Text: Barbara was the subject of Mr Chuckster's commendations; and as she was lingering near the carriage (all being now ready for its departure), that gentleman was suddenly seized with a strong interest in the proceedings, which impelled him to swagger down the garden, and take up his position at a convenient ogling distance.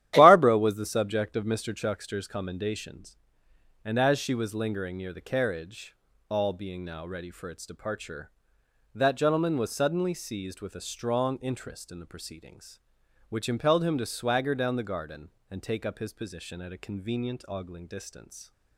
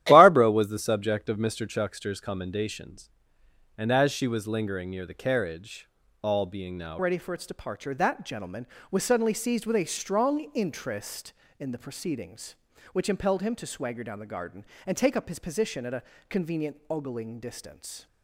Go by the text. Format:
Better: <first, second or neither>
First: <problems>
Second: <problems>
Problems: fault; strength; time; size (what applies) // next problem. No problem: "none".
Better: first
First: starts louder than the rest; strong; until 1.1 s; 12 dB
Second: starts louder than the rest; strong; until 1.0 s; 12.5 dB // changes voice at "ready"; from 6.9 s on; 11.1 s long // pauses between "a" and "convenient"; slight; at 16.0 s; 0.28 s long